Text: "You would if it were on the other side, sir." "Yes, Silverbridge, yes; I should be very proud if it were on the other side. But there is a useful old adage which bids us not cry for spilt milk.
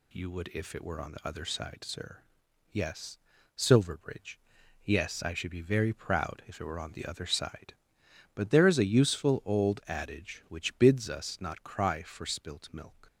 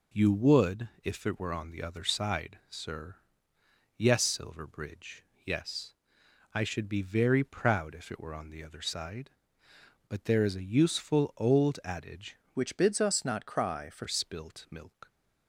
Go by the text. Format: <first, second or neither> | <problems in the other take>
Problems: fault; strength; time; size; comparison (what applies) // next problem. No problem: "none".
first | changes voice from "which" to "for"; from 12.5 to 14.0 s; 1.5 s long